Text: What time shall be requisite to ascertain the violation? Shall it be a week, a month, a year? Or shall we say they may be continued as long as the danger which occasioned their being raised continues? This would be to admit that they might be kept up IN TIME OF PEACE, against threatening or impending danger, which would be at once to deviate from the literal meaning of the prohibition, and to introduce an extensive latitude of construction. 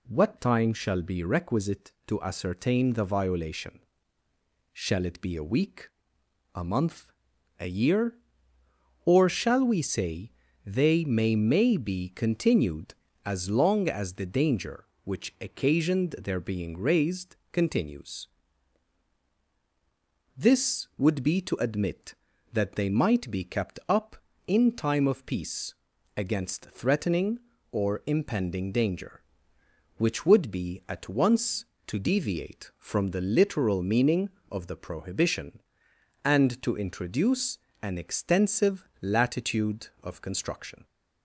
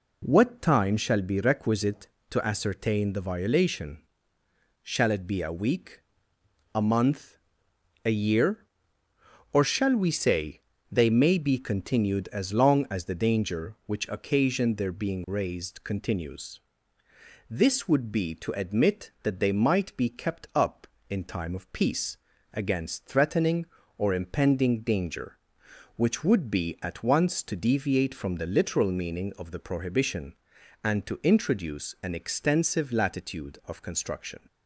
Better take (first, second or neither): second